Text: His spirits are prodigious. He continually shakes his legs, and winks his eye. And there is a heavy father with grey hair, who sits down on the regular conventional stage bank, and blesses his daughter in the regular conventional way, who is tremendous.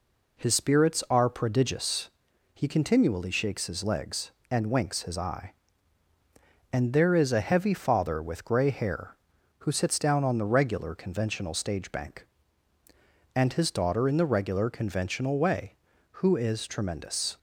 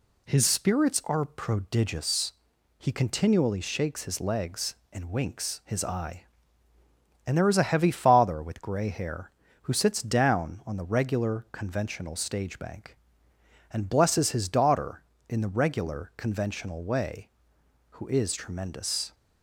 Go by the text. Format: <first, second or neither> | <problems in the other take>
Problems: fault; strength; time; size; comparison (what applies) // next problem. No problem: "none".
second | skips "blesses"; at 13.5 s